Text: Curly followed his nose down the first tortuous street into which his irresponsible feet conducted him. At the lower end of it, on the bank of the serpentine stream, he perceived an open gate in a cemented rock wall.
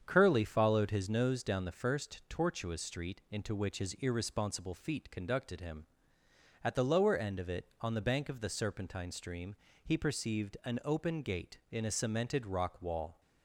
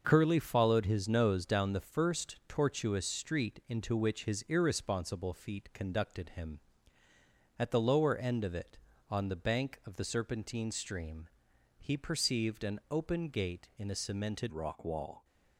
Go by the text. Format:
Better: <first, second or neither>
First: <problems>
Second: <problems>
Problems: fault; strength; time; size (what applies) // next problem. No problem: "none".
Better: first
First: starts louder than the rest; strong; until 1.0 s; 7.5 dB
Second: starts louder than the rest; until 1.0 s; 6 dB // changes voice at "rock"; from 14.5 s on; 0.7 s long